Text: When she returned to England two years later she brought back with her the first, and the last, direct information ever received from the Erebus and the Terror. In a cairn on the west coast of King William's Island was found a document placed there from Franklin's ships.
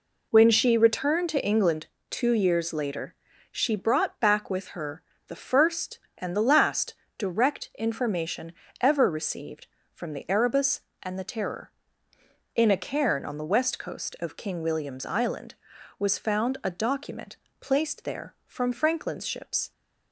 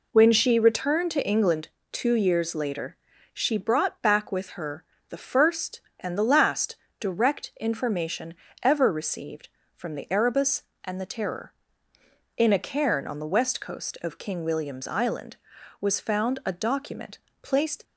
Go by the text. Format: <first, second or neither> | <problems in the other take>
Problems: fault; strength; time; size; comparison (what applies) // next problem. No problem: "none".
first | pauses between "England" and "two"; slight; at 1.6 s; 0.22 s long; slight in the first // pauses between "later" and "she"; at 2.9 s; 0.38 s long; also in the first // pauses between "her" and "the"; slight; at 4.8 s; 0.24 s long; slight in the first // pauses between "information" and "ever"; slight; at 8.3 s; 0.28 s long; slight in the first // pauses between "document" and "placed"; slight; at 17.1 s; 0.24 s long; slight in the first // stops before "there from Franklin's ships"; at 17.8 s